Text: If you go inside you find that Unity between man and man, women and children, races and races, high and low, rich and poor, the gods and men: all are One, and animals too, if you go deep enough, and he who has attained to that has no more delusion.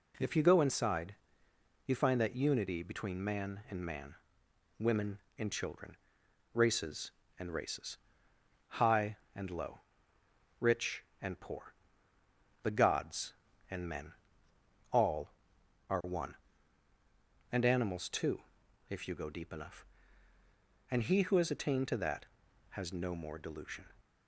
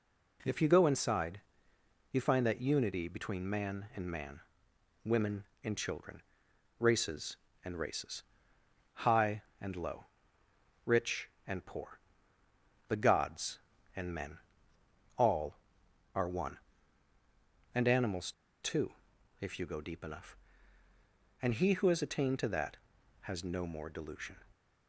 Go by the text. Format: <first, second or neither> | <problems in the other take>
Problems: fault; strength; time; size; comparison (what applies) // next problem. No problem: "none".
first | pauses between "inside" and "you"; noticeable; at 1.4 s; 0.70 s long; noticeable in the first // pauses between "animals" and "too"; slight; at 18.3 s; 0.29 s long